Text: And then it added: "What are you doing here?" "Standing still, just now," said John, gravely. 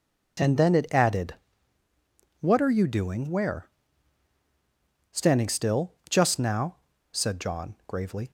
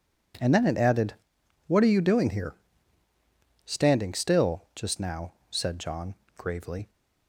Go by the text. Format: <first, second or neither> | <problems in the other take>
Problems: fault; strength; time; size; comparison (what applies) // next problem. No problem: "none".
second | says "where" for "here"; at 3.2 s